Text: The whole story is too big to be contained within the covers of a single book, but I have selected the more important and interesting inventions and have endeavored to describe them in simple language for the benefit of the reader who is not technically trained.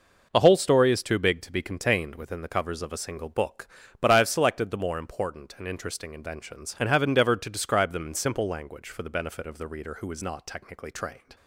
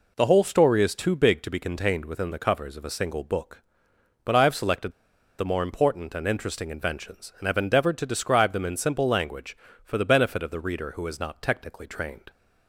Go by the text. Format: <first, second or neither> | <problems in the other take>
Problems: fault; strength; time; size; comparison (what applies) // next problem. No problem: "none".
first | pauses between "selected" and "the"; noticeable; at 4.9 s; 0.46 s long